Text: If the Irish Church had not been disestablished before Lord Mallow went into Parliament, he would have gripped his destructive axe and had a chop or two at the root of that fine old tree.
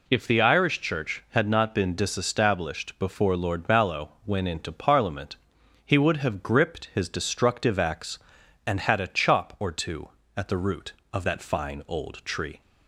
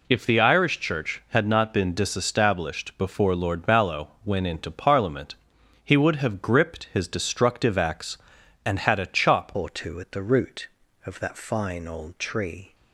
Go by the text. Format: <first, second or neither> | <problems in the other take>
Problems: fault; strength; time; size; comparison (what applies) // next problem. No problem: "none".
first | changes voice at "or"; from 9.5 s on; 3.2 s long